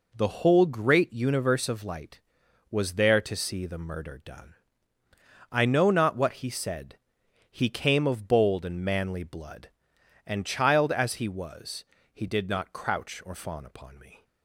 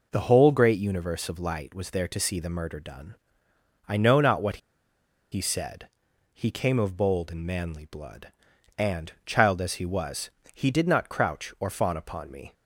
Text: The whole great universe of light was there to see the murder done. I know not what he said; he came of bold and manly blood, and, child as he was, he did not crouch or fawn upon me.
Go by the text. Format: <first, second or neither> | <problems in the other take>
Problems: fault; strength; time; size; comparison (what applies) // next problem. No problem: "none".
first | pauses between "what" and "he"; noticeable; at 4.5 s; 0.74 s long